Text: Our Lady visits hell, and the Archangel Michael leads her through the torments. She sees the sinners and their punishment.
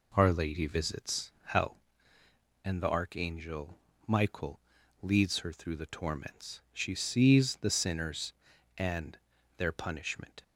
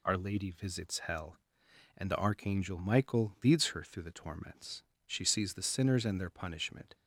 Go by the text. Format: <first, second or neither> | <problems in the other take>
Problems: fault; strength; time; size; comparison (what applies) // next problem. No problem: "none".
second | starts louder than the rest; slight; until 1.8 s; 3.5 dB // pauses between "Archangel" and "Michael"; slight; at 3.7 s; 0.28 s long // pauses between "Michael" and "leads"; at 4.5 s; 0.42 s long // pauses between "and" and "their"; at 9.1 s; 0.40 s long